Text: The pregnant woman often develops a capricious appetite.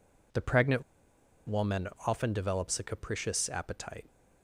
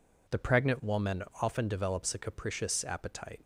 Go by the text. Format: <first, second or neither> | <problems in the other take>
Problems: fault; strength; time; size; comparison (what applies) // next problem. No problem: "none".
second | pauses between "pregnant" and "woman"; noticeable; at 0.8 s; 0.64 s long // pauses between "woman" and "often"; slight; at 1.8 s; 0.18 s long; slight in the second